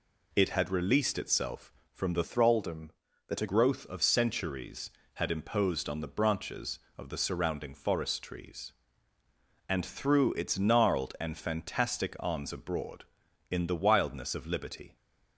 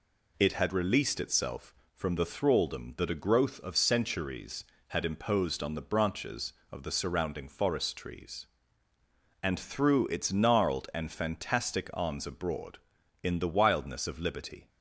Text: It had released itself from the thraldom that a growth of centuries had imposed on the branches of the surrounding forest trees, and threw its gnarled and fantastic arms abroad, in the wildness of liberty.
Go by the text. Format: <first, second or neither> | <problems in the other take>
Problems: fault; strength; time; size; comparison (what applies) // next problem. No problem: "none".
second | changes voice from "thraldom" to "a"; from 2.2 to 3.4 s; 1.2 s long